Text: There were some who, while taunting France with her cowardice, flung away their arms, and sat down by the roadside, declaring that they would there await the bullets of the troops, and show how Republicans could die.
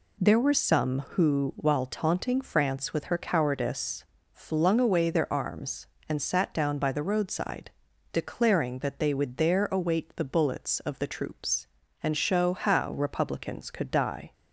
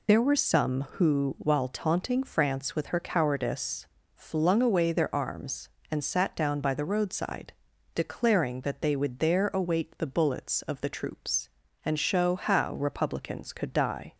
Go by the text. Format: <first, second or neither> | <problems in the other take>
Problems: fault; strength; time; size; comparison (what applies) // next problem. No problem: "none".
first | loses the start of "There"; at 0.0 s; 85 ms